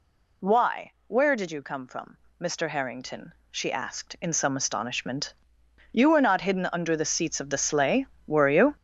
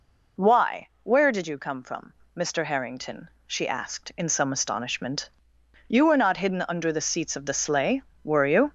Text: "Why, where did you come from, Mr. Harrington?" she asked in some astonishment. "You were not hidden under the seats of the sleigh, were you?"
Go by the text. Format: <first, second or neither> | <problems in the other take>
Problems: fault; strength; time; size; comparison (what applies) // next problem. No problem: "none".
second | gets louder; strong; throughout; 9.5 dB